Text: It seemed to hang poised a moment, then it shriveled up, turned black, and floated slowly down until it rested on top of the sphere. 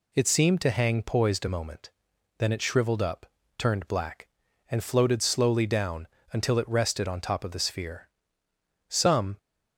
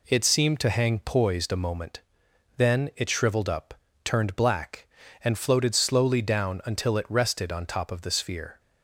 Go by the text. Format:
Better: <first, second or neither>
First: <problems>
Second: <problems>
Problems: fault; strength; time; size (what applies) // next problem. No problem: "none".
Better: second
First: pauses between "down" and "until"; slight; at 6.0 s; 0.26 s long // goes on to say "Some"; slight; from 8.8 s on; 0.48 s long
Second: none